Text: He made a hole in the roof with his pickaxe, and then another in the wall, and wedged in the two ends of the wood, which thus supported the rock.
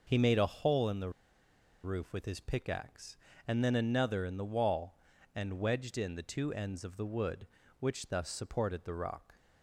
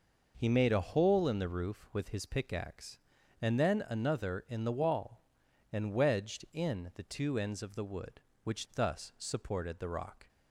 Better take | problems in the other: second | pauses between "the" and "roof"; noticeable; at 1.0 s; 0.73 s long

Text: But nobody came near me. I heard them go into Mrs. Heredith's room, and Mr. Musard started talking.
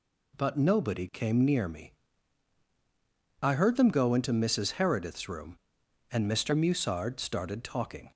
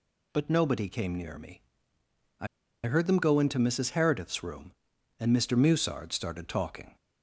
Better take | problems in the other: first | pauses between "I" and "heard"; at 2.4 s; 0.38 s long

